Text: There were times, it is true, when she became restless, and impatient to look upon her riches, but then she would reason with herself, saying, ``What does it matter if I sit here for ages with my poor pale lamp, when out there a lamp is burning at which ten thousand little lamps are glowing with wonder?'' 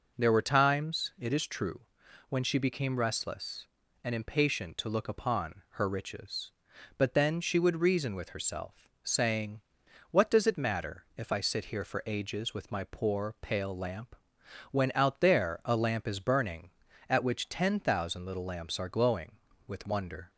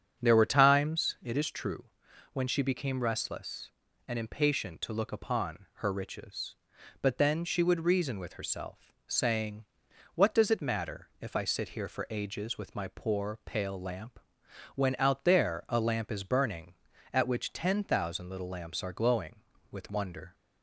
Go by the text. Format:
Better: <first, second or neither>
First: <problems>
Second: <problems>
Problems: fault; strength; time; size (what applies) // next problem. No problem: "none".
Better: first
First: none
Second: starts louder than the rest; strong; until 1.3 s; 8 dB